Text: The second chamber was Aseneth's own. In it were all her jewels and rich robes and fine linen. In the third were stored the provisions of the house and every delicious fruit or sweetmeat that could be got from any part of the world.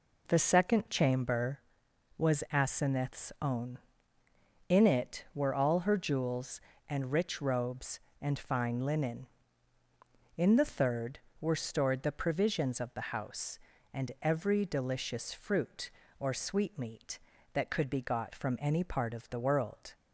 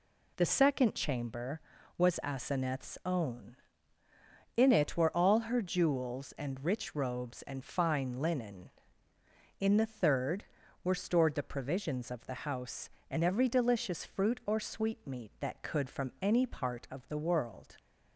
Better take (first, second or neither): first